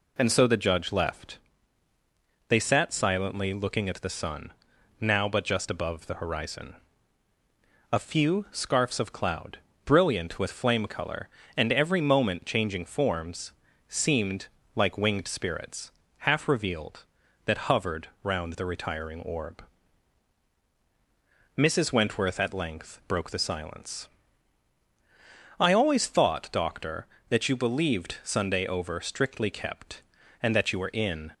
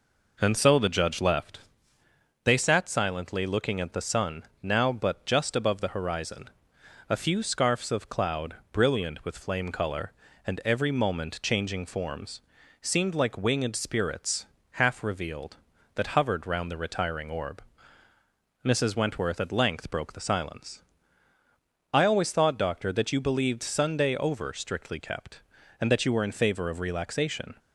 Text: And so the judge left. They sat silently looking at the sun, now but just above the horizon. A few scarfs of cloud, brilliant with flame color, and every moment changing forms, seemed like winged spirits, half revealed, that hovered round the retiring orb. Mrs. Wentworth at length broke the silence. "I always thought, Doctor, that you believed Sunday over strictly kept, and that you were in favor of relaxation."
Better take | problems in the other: second | pauses between "seemed" and "like"; slight; at 14.4 s; 0.28 s long // pauses between "hovered" and "round"; slight; at 18.0 s; 0.16 s long // stops before "favor of relaxation"; at 31.3 s

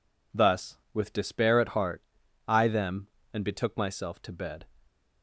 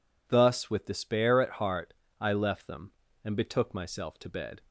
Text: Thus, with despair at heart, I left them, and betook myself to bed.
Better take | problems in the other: second | skips "left"; at 2.6 s

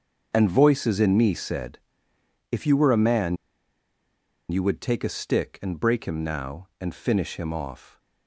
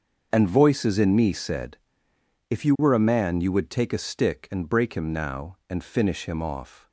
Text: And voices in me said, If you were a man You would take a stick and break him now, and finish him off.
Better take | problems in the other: second | starts louder than the rest; until 1.3 s; 6.5 dB; also in the second // pauses between "man" and "You"; at 3.3 s; 1.1 s long

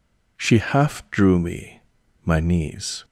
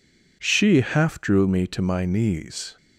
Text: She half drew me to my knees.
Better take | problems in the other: second | skips "to"; at 2.0 s

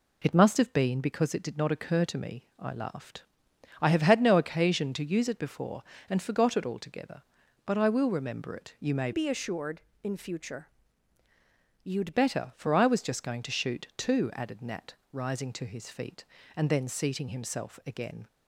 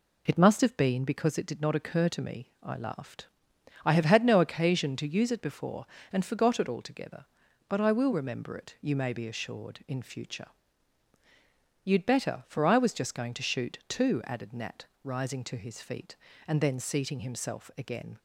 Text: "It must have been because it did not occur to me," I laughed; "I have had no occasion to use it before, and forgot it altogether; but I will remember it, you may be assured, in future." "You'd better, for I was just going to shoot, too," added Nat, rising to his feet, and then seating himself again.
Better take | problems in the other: second | changes voice from "be" to "You'd"; from 9.1 to 12.1 s; 3.0 s long

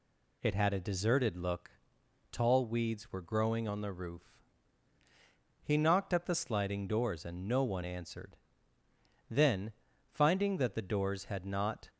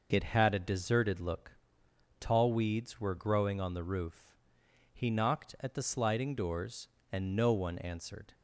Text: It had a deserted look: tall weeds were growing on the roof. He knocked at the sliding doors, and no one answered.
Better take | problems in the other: second | goes on to say "Then finding that the doors had not"; strong; from 9.3 s on; 2.5 s long

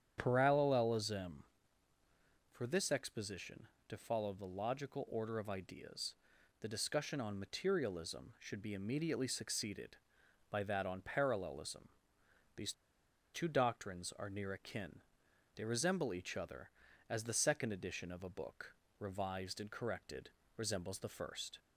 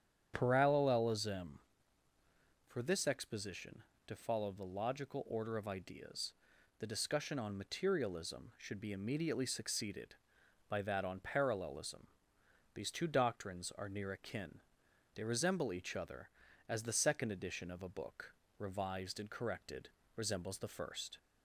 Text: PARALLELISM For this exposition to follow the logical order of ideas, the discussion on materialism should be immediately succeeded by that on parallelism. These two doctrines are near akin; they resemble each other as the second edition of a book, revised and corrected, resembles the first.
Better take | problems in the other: second | starts louder than the rest; strong; until 1.1 s; 9 dB; strong in the second // pauses between "These" and "two"; noticeable; at 12.7 s; 0.60 s long

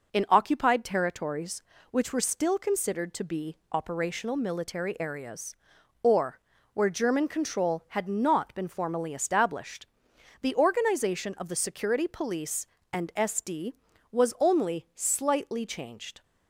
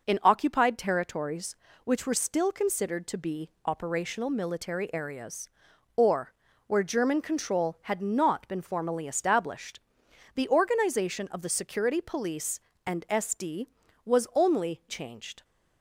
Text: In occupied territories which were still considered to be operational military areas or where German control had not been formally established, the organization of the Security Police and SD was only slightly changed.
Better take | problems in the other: first | pauses between "be" and "operational"; slight; at 3.4 s; 0.16 s long; slight in the first // pauses between "or" and "where"; slight; at 6.3 s; 0.34 s long; slight in the first // skips "slightly"; at 14.8 s

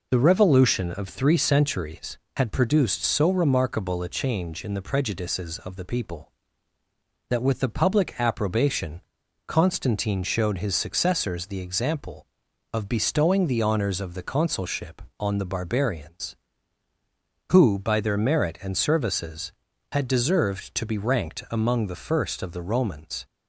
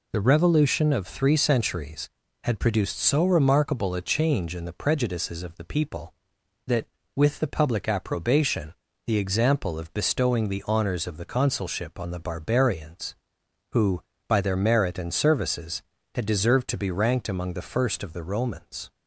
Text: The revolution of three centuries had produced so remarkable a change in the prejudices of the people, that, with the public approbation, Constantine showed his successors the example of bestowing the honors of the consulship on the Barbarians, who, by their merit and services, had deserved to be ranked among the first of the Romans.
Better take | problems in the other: first | skips "Constantine showed his successors"; at 8.9 s

